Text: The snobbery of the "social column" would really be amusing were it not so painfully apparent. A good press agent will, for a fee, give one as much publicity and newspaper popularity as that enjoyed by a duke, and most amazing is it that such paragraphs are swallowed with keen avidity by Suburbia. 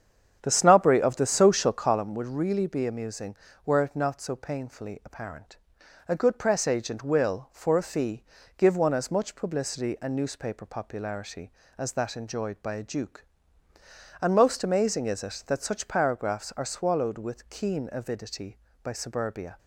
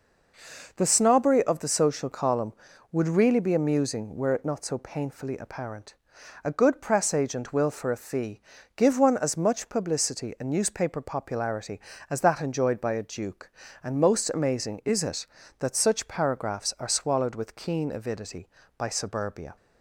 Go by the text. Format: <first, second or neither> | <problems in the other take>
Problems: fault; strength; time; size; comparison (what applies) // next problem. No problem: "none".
second | starts louder than the rest; strong; until 2.0 s; 8 dB